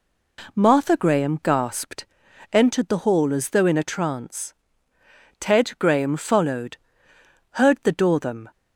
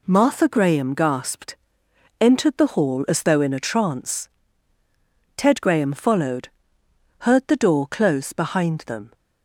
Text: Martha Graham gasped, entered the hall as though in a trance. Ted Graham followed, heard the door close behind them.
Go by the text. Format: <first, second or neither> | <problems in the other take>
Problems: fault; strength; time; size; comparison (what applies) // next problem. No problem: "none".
second | skips "close behind"; at 8.1 s